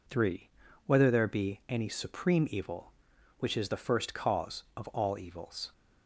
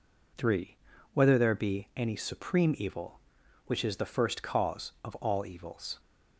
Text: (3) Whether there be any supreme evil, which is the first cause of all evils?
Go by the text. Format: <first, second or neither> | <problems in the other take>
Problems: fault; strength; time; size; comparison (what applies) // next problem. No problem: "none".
neither | none